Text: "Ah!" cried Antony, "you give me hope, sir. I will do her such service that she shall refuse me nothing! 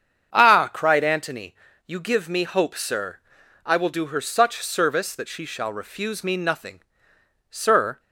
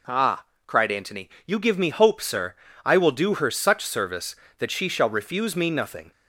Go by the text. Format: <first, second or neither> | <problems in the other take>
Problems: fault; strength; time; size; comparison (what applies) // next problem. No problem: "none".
second | starts louder than the rest; strong; until 1.3 s; 7.5 dB // goes on to say "Sir"; from 7.4 s on; 0.50 s long